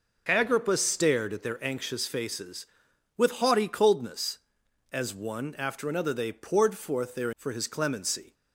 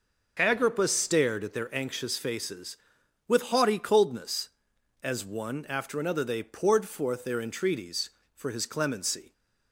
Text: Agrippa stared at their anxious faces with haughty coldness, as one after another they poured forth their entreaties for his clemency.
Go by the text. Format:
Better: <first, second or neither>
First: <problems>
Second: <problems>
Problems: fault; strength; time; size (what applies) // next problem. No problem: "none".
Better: second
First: skips "entreaties"; at 7.3 s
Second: none